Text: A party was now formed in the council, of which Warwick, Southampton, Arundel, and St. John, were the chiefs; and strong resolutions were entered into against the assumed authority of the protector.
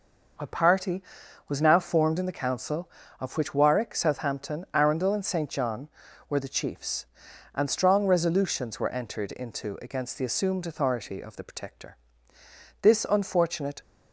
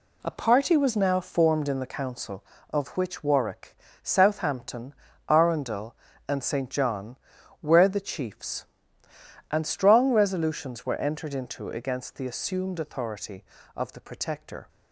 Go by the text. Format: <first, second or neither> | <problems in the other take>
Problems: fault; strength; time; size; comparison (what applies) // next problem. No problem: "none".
second | goes on to say "This unfortunate"; noticeable; from 12.8 s on; 0.98 s long